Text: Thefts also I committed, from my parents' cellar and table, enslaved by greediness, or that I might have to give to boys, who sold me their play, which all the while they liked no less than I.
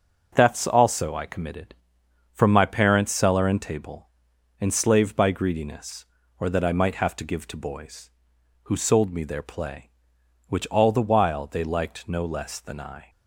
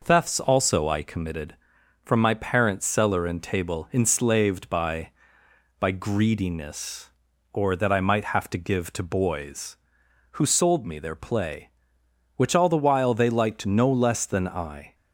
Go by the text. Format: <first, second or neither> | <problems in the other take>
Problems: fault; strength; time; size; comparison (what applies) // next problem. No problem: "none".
first | says "by" twice; at 5.7 s